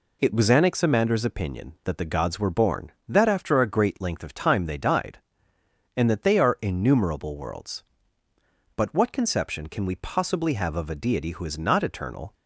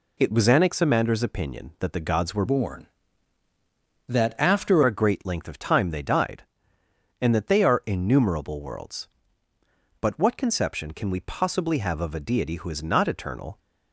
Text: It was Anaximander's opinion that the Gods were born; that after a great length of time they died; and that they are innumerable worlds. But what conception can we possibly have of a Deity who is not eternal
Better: first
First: none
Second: changes voice from "born" to "after"; from 2.4 to 4.8 s; 2.4 s long

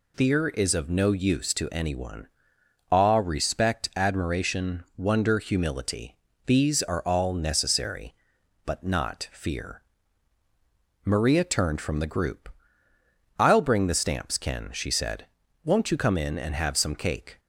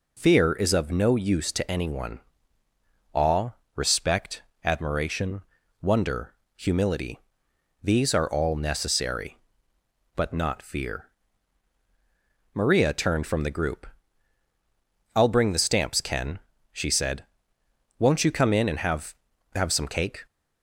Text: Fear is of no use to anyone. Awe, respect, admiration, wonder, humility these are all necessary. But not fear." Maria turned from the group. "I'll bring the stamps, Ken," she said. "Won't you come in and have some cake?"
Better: first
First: pauses between "humility" and "these"; slight; at 6.1 s; 0.34 s long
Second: pauses between "humility" and "these"; noticeable; at 7.1 s; 0.64 s long // says "have" twice; at 19.5 s

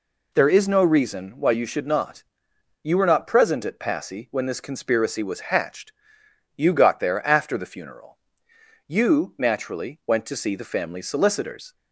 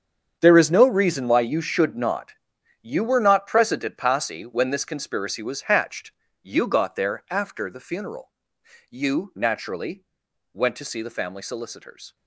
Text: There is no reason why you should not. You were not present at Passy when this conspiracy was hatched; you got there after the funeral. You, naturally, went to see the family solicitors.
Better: first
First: none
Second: gets quieter; strong; throughout; 14.5 dB

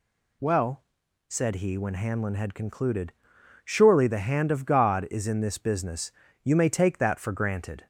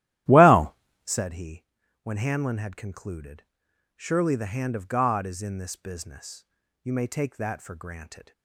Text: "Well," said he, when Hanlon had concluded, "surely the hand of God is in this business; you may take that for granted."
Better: first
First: none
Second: starts louder than the rest; strong; until 1.2 s; 13.5 dB

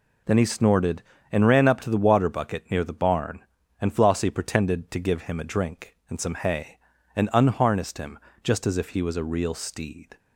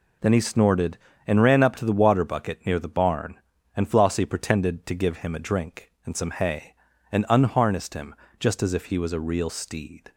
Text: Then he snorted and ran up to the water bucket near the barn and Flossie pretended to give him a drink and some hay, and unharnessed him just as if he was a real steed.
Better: neither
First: pauses between "him" and "just"; slight; at 8.1 s; 0.24 s long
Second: pauses between "him" and "just"; slight; at 8.1 s; 0.24 s long

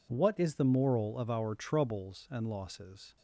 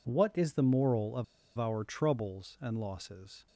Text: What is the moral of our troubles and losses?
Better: first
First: none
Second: pauses between "of" and "our"; slight; at 1.2 s; 0.33 s long

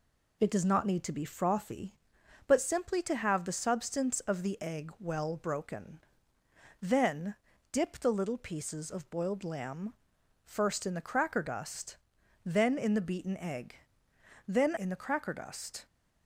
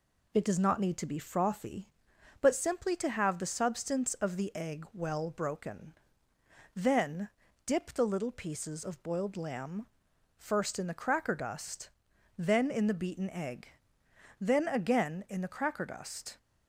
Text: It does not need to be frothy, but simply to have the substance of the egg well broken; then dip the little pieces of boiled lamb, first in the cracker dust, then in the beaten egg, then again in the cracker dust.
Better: second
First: pauses between "then" and "dip"; at 7.3 s; 0.38 s long // skips "again"; at 14.7 s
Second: pauses between "then" and "dip"; at 7.2 s; 0.38 s long

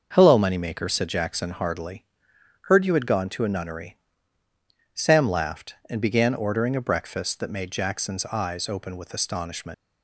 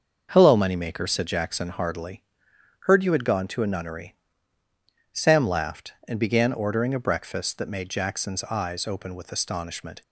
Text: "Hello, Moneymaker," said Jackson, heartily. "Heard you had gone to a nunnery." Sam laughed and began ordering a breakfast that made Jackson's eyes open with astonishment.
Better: second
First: starts louder than the rest; until 1.1 s; 6.5 dB // leaves "astonishment" unfinished; at 9.7 s; 90 ms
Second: starts louder than the rest; until 1.3 s; 6.5 dB

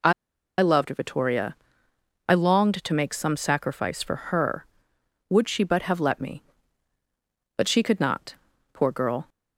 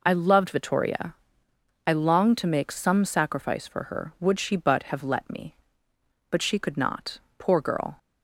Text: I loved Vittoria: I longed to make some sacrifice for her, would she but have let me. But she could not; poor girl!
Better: second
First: pauses between "I" and "loved"; noticeable; at 0.1 s; 0.47 s long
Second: none

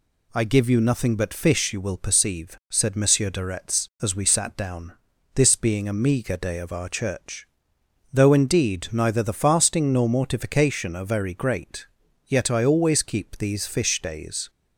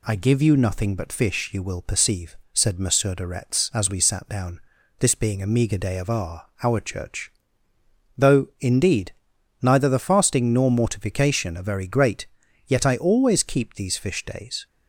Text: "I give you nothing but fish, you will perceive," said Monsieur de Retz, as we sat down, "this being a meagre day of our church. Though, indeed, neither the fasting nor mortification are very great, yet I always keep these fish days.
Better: first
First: none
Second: says "our" twice; at 6.6 s

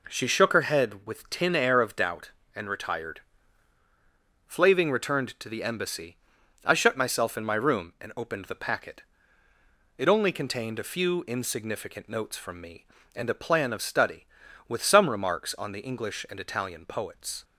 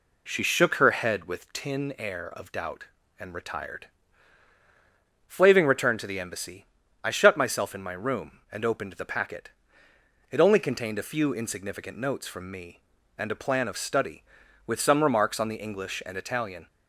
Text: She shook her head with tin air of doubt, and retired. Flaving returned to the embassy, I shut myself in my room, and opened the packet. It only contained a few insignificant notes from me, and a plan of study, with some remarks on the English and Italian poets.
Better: first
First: none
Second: stops before "poets"; at 16.6 s

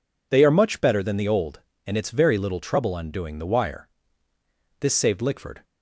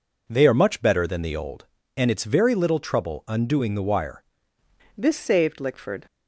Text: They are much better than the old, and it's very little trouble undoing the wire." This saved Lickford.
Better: first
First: none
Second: changes voice at "This"; from 4.9 s on; 1.1 s long

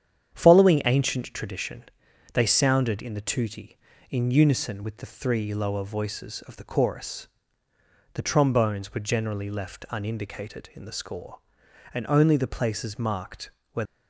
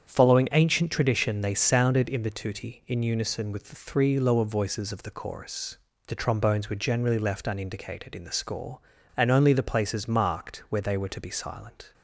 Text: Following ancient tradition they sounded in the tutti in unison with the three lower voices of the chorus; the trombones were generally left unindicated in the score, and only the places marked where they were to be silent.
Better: second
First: starts louder than the rest; strong; until 1.3 s; 9 dB // pauses between "tradition" and "they"; noticeable; at 1.8 s; 0.50 s long // pauses between "marked" and "where"; slight; at 13.4 s; 0.22 s long // stops before "they were to be silent"; at 13.8 s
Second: starts louder than the rest; strong; until 1.1 s; 8 dB

